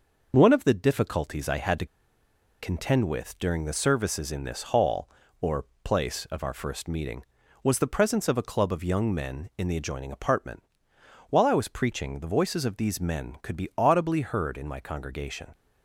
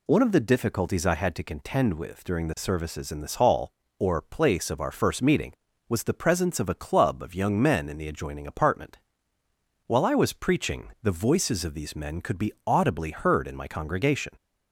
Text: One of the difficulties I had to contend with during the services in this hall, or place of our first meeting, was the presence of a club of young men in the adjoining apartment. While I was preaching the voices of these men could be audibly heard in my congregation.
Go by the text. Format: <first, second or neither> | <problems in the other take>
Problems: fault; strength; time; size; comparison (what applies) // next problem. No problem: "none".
second | pauses between "to" and "contend"; noticeable; at 1.8 s; 0.75 s long // pauses between "or" and "place"; slight; at 5.6 s; 0.18 s long